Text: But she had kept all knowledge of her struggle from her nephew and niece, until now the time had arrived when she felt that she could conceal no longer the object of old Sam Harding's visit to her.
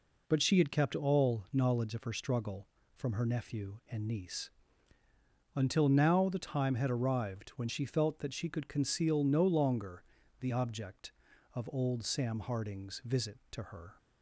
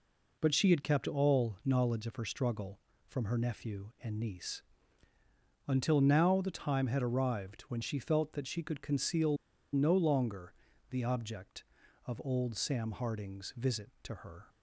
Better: first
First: pauses between "longer" and "the"; at 10.0 s; 0.38 s long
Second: pauses between "conceal" and "no"; at 9.3 s; 0.37 s long // pauses between "longer" and "the"; at 10.5 s; 0.38 s long

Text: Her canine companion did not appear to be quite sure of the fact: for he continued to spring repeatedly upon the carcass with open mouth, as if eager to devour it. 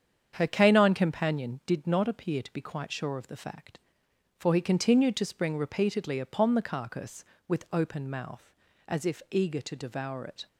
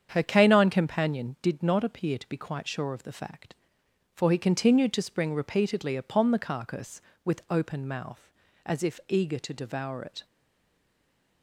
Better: first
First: starts louder than the rest; strong; until 1.3 s; 8 dB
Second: starts louder than the rest; strong; until 1.1 s; 8 dB // stays silent after the last word; noticeable; from 10.2 s on; 1.2 s long

